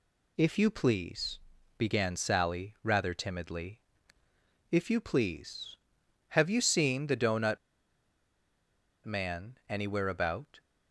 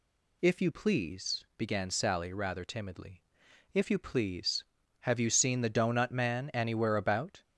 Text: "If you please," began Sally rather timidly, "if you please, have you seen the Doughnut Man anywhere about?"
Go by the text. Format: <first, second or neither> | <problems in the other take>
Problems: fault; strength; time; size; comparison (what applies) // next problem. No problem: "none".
second | pauses between "Doughnut" and "Man"; strong; at 7.5 s; 1.4 s long